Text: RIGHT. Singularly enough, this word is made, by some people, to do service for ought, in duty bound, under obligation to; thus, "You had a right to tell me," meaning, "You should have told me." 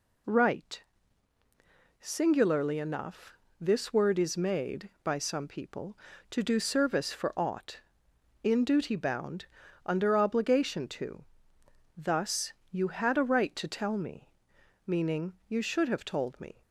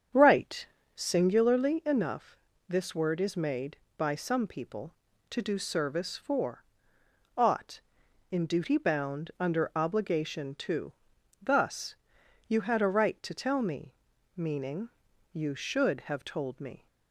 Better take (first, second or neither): first